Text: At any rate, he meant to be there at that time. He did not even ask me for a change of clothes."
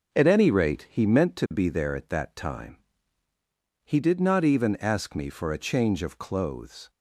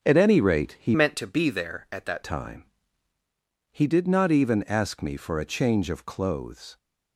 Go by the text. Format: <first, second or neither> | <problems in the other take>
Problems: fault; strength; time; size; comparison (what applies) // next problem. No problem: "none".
first | starts louder than the rest; until 1.0 s; 6.5 dB // changes voice from "meant" to "that"; from 0.9 to 2.2 s; 1.3 s long